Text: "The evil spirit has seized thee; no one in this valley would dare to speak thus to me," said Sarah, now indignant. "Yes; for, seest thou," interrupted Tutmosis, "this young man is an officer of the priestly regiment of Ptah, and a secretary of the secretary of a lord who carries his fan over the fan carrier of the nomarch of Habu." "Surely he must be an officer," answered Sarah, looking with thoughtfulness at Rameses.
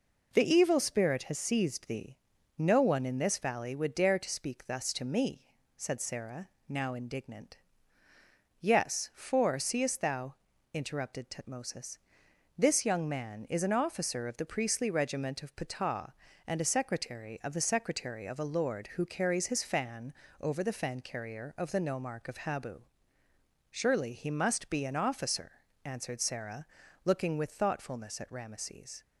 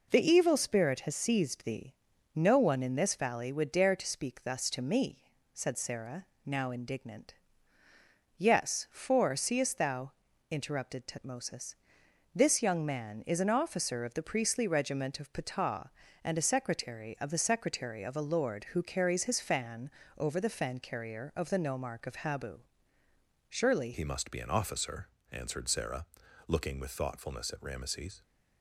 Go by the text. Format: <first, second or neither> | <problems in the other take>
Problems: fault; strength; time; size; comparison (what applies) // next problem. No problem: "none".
first | pauses between "fan" and "over"; slight; at 19.8 s; 0.26 s long; slight in the first // changes voice at "he"; from 23.9 s on; 4.3 s long